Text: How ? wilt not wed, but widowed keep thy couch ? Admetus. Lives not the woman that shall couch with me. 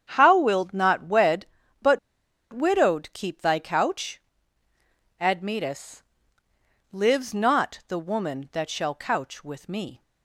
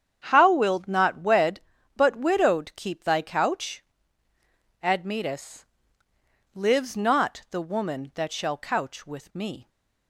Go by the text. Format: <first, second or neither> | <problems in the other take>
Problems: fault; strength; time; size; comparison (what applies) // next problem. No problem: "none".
second | starts louder than the rest; strong; until 1.1 s; 8 dB; strong in the second // pauses between "but" and "widowed"; noticeable; at 1.9 s; 0.53 s long